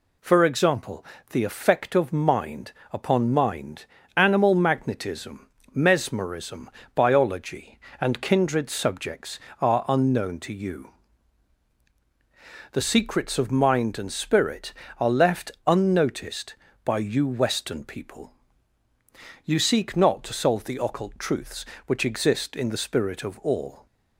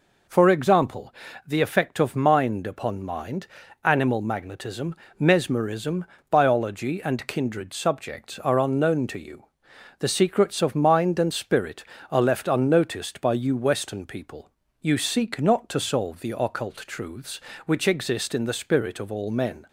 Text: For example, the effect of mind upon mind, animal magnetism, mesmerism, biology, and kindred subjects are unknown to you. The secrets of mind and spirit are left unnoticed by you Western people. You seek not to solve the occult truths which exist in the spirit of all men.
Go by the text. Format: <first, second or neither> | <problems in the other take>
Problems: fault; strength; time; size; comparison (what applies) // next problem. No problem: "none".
second | pauses between "mind" and "upon"; slight; at 2.7 s; 0.20 s long // pauses between "left" and "unnoticed"; slight; at 15.5 s; 0.15 s long // stops before "men"; at 23.8 s